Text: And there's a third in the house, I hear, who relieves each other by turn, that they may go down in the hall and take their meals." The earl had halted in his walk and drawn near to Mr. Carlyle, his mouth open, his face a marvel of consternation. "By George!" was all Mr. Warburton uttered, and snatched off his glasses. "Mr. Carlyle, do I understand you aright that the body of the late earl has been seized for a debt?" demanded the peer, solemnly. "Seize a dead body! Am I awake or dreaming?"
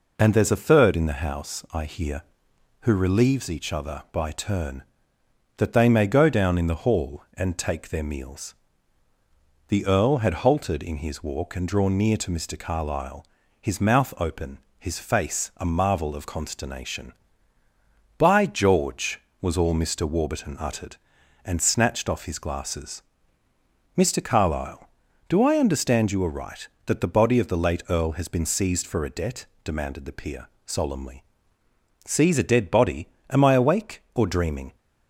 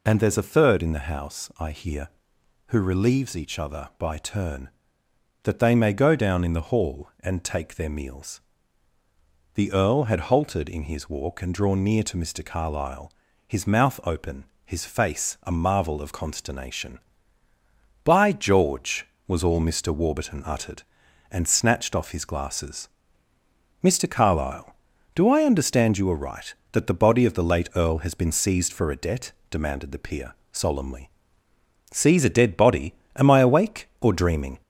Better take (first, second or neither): first